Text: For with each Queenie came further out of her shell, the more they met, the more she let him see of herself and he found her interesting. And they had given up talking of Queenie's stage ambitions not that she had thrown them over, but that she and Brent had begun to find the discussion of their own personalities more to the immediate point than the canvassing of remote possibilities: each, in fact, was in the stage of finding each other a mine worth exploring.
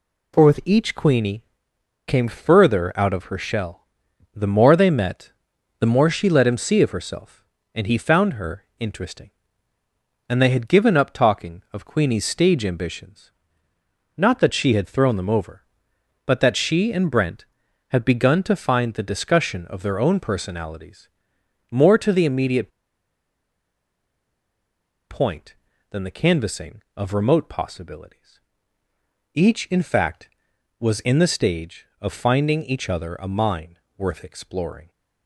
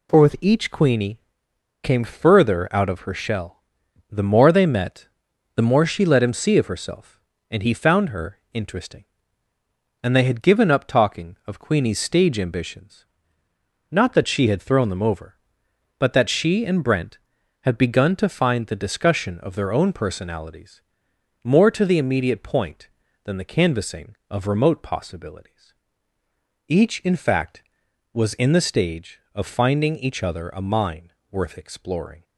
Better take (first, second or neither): second